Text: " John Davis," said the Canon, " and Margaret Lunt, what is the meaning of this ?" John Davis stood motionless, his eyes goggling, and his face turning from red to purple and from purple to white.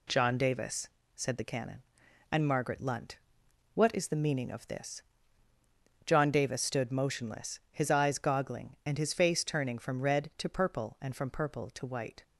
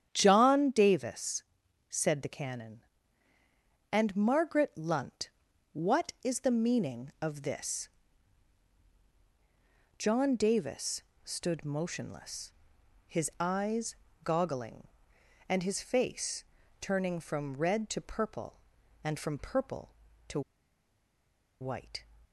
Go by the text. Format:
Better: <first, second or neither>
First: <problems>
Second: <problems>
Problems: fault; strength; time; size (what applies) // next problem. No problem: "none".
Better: first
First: none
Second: starts louder than the rest; strong; until 1.1 s; 9 dB // pauses between "Davis" and "stood"; slight; at 11.0 s; 0.22 s long // pauses between "eyes" and "goggling"; slight; at 13.9 s; 0.28 s long // pauses between "face" and "turning"; at 16.4 s; 0.38 s long // pauses between "to" and "white"; at 20.4 s; 1.2 s long